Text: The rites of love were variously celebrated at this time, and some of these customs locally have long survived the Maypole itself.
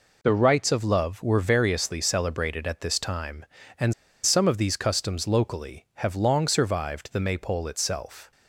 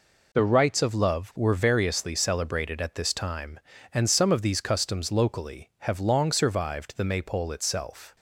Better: second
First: pauses between "and" and "some"; slight; at 3.9 s; 0.31 s long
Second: none

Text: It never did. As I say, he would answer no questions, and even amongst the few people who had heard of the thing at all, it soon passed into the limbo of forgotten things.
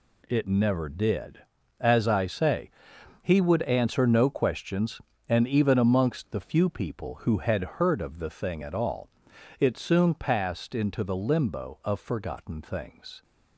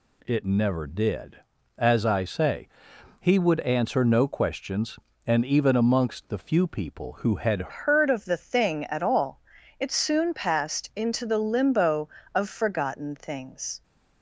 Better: first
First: none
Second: changes voice at "heard"; from 7.6 s on; 6.2 s long

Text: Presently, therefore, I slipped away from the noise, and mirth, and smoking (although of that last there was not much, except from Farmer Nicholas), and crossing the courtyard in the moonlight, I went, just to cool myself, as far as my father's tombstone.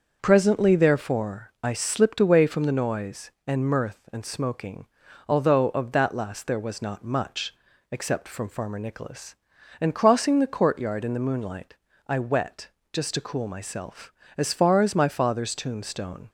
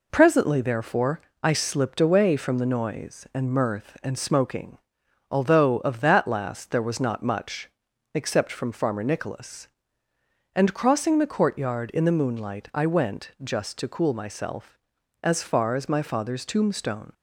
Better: second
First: starts louder than the rest; until 1.2 s; 6.5 dB // says "wet" for "went"; at 12.1 s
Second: none

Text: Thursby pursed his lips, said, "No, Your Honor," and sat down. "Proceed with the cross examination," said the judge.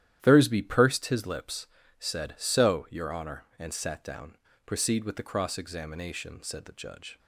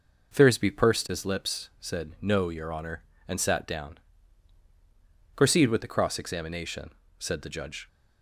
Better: second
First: starts louder than the rest; strong; until 1.2 s; 11.5 dB // says "So" for "No"; at 2.3 s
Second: none

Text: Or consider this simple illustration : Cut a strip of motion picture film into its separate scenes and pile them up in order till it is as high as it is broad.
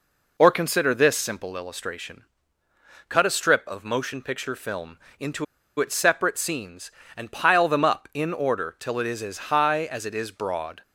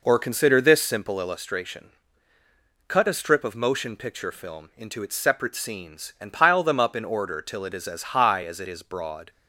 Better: second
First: pauses between "film" and "into"; slight; at 4.9 s; 0.20 s long // pauses between "into" and "its"; slight; at 5.4 s; 0.35 s long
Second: none

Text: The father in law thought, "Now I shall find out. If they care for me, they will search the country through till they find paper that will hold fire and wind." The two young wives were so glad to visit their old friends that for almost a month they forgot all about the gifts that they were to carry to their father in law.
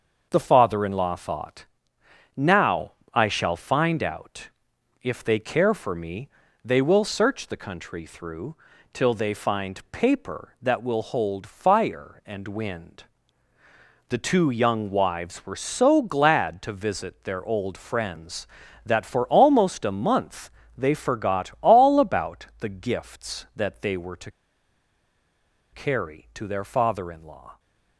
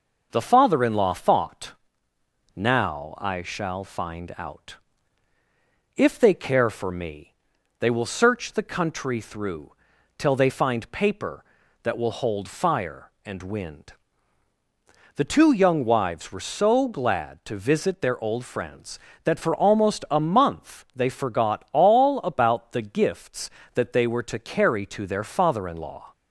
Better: second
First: starts louder than the rest; until 1.3 s; 6.5 dB // pauses between "Now" and "I"; slight; at 2.9 s; 0.22 s long // pauses between "through" and "till"; at 8.5 s; 0.38 s long // pauses between "month" and "they"; slight; at 20.5 s; 0.26 s long // pauses between "to" and "carry"; strong; at 24.3 s; 1.4 s long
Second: pauses between "through" and "till"; noticeable; at 9.7 s; 0.46 s long

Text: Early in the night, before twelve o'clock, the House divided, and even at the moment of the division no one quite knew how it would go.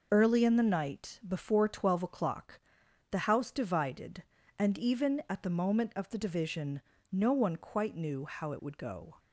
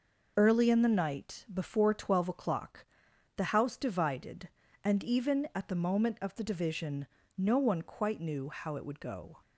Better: neither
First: pauses between "division" and "no"; slight; at 6.8 s; 0.30 s long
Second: pauses between "division" and "no"; slight; at 7.0 s; 0.30 s long

